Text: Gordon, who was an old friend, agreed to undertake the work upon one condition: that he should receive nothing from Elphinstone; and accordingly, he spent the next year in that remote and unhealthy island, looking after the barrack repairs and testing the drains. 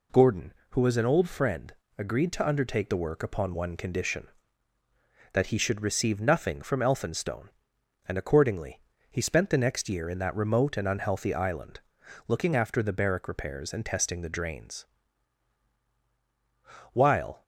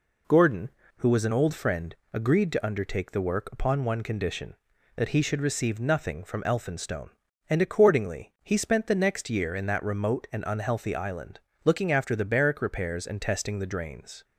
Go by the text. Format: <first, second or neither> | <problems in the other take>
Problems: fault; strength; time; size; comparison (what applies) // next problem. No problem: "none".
second | goes on to say "While"; from 16.9 s on; 0.50 s long